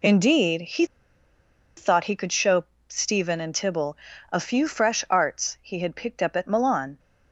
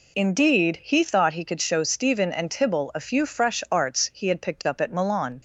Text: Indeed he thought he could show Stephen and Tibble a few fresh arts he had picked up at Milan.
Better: second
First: pauses between "he" and "thought"; noticeable; at 0.8 s; 0.92 s long // pauses between "show" and "Stephen"; slight; at 2.6 s; 0.22 s long // pauses between "Tibble" and "a"; slight; at 3.9 s; 0.34 s long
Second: none

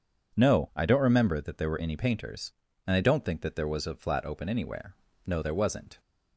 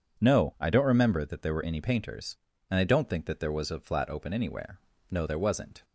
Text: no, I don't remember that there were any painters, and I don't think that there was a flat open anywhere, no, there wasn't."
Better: neither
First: none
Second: none

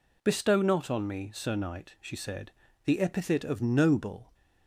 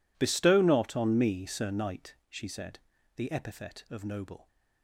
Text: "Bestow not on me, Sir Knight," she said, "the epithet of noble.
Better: neither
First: none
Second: none

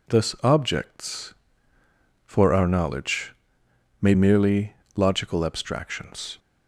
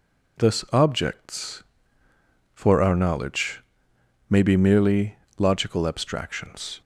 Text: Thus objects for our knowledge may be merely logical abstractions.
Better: second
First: pauses between "knowledge" and "may"; noticeable; at 3.3 s; 0.70 s long // skips "be"; at 4.1 s // pauses between "merely" and "logical"; slight; at 4.7 s; 0.22 s long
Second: pauses between "knowledge" and "may"; noticeable; at 3.6 s; 0.70 s long // pauses between "merely" and "logical"; slight; at 5.1 s; 0.22 s long

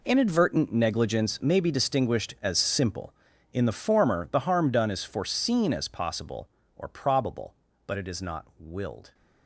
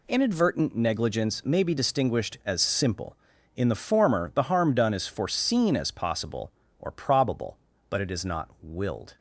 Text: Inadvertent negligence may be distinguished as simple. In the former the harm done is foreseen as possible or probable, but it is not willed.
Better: second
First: gets quieter; strong; throughout; 14.5 dB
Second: none

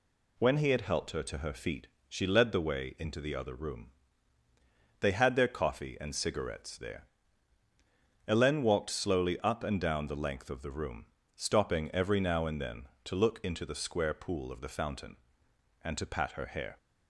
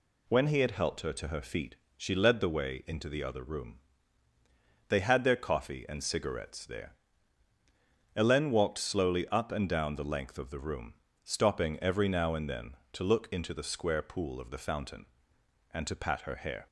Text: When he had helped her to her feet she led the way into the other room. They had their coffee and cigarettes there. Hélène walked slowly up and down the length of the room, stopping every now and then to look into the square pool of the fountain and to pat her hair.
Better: neither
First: pauses between "feet" and "she"; slight; at 1.8 s; 0.22 s long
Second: pauses between "feet" and "she"; slight; at 1.7 s; 0.22 s long

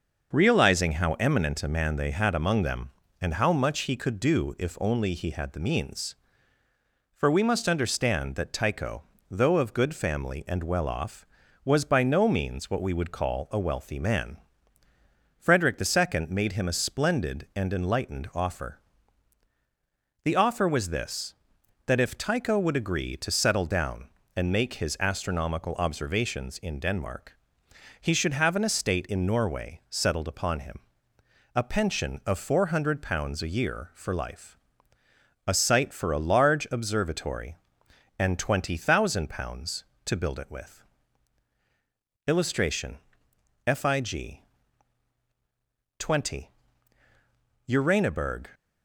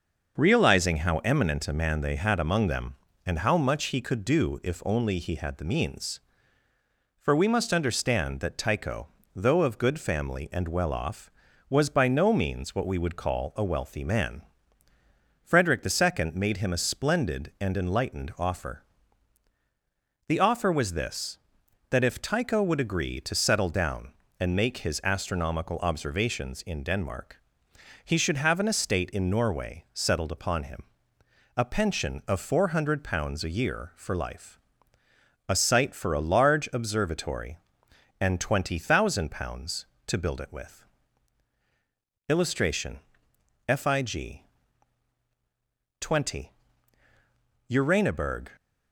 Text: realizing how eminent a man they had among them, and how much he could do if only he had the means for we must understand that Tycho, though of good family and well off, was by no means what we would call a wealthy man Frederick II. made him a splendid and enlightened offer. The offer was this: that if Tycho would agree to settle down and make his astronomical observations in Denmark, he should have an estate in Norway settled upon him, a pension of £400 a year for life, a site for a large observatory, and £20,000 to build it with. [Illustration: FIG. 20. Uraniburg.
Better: neither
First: pauses between "man" and "Frederick"; at 14.3 s; 1.0 s long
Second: pauses between "man" and "Frederick"; at 14.4 s; 1.0 s long

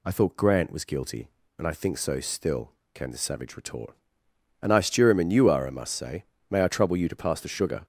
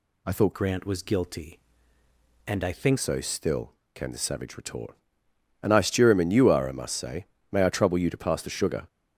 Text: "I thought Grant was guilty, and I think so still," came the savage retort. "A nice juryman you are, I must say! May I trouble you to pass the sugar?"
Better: first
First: none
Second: changes voice from "Grant" to "think"; from 0.5 to 2.9 s; 2.4 s long

